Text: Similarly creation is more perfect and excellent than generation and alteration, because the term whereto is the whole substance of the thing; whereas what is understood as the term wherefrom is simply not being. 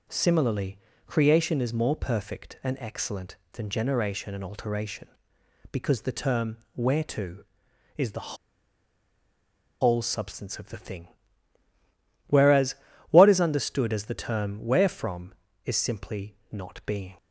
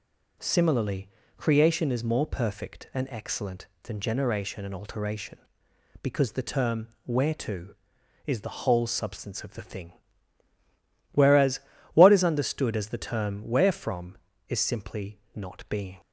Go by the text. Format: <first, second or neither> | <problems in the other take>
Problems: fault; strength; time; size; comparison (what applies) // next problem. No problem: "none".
second | pauses between "Similarly" and "creation"; slight; at 0.7 s; 0.28 s long; slight in the second // pauses between "term" and "whereto"; slight; at 6.5 s; 0.18 s long; slight in the second // pauses between "the" and "whole"; strong; at 8.3 s; 1.4 s long // pauses between "whereas" and "what"; slight; at 12.7 s; 0.36 s long; slight in the second